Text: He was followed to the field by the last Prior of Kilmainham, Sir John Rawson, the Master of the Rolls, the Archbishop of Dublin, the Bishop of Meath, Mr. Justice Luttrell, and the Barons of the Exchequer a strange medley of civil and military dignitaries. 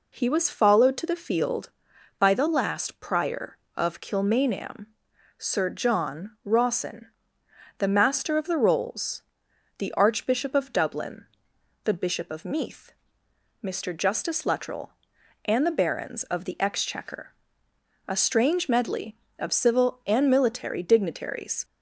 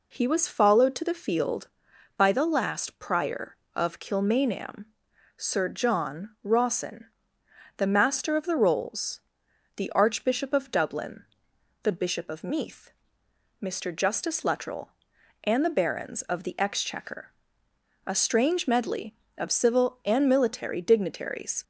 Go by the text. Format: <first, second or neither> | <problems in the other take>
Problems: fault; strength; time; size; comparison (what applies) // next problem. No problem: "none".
neither | pauses between "Exchequer" and "a"; noticeable; the same in both